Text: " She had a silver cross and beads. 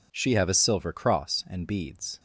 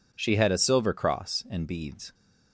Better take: second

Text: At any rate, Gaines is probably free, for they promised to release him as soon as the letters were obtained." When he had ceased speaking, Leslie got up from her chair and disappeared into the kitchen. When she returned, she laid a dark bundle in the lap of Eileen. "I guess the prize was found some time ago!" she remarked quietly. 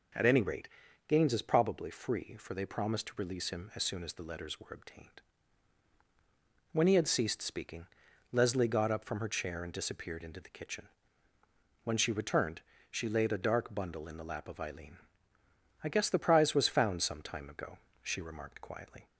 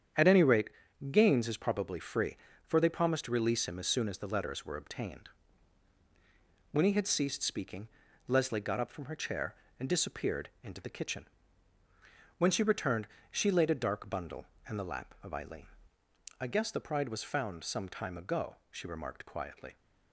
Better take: first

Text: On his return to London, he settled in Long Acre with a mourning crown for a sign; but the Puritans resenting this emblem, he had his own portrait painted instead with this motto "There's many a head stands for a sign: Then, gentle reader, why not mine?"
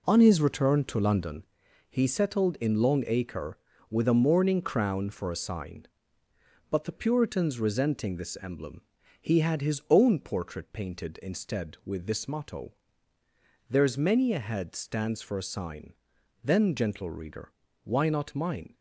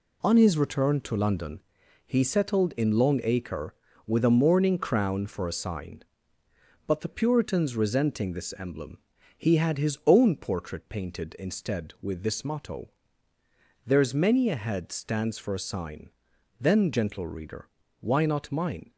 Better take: second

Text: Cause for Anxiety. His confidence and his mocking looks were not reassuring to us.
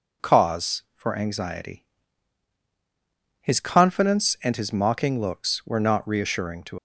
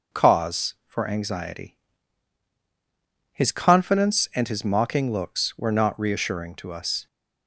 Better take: second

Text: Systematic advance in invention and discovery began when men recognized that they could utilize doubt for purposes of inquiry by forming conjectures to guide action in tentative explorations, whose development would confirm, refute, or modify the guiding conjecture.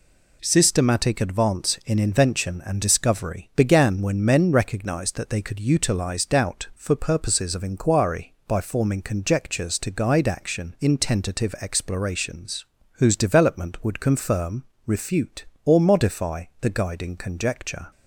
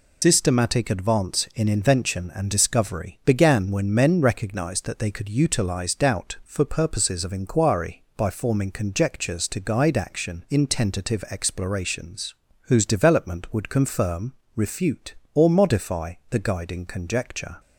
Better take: first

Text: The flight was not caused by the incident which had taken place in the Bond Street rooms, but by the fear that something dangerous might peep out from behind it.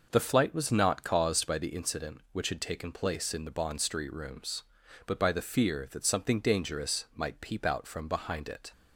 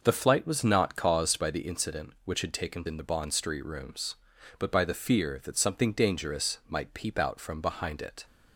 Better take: first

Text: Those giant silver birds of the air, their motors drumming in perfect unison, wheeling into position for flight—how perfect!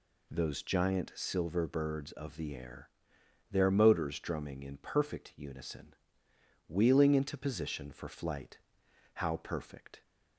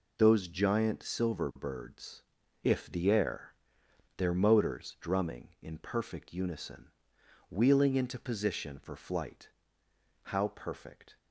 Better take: first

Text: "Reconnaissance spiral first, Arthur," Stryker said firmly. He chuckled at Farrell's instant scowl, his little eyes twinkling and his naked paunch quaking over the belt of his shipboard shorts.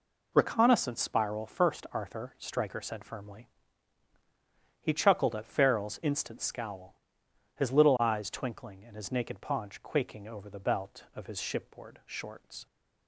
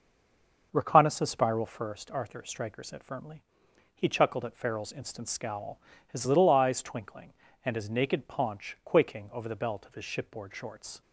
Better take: first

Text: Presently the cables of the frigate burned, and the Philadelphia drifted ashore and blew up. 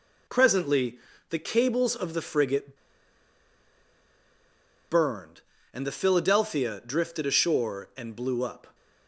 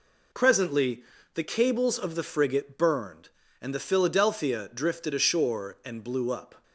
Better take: second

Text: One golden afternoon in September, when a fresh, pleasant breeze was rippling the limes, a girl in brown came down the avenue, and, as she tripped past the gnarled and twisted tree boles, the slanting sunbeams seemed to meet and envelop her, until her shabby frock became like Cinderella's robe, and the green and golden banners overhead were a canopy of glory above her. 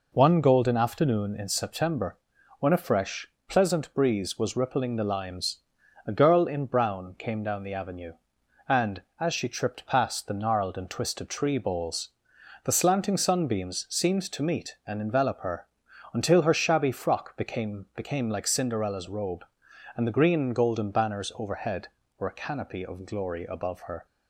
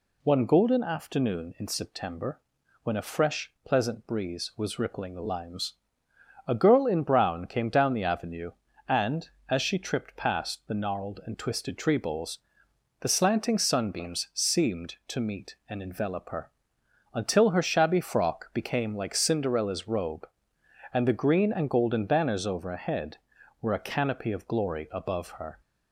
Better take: second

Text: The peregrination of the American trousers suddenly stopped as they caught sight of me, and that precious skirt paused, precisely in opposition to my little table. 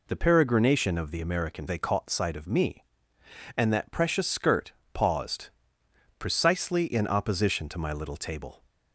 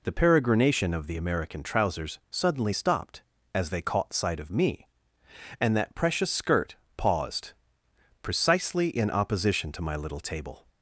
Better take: second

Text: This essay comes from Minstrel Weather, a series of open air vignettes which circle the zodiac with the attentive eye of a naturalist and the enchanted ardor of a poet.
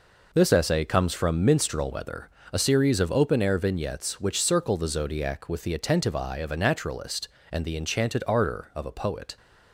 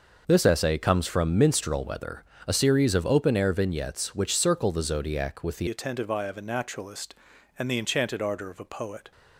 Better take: first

